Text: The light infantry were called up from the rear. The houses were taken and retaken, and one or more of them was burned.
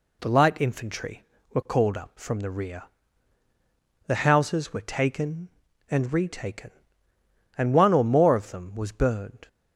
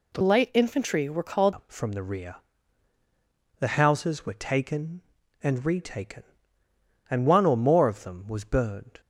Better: first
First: none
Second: changes voice from "light" to "called"; from 0.2 to 1.5 s; 1.3 s long

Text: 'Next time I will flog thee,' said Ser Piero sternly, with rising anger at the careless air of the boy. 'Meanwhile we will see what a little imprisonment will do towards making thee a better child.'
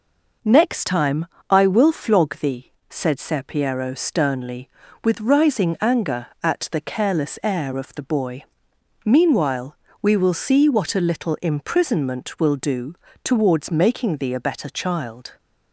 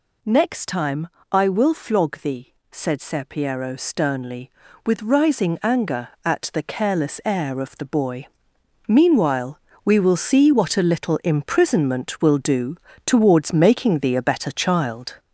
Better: first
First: pauses between "time" and "I"; slight; at 1.2 s; 0.26 s long // pauses between "Meanwhile" and "we"; slight; at 9.7 s; 0.24 s long // pauses between "do" and "towards"; slight; at 12.9 s; 0.30 s long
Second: gets louder; noticeable; throughout; 4.5 dB // pauses between "time" and "I"; slight; at 1.0 s; 0.26 s long // pauses between "Meanwhile" and "we"; slight; at 9.5 s; 0.24 s long // pauses between "do" and "towards"; slight; at 12.7 s; 0.30 s long

